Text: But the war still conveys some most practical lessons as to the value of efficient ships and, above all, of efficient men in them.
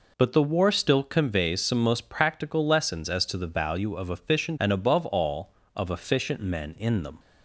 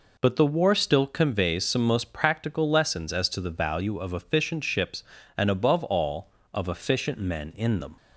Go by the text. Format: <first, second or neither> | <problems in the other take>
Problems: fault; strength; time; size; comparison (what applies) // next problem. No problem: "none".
second | skips "ships"; at 4.5 s